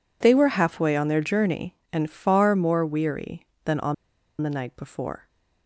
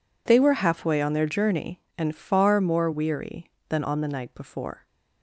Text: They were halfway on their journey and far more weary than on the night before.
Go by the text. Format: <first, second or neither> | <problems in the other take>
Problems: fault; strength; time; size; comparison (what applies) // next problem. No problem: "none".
second | pauses between "on" and "the"; noticeable; at 3.9 s; 0.47 s long